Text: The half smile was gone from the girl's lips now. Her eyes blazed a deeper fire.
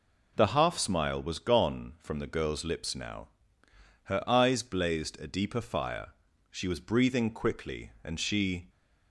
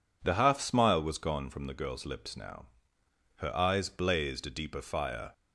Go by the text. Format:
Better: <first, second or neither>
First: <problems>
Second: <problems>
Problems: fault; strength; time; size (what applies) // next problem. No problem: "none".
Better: second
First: goes on to say "She was breathing quickly and she"; strong; from 6.4 s on; 2.2 s long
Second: none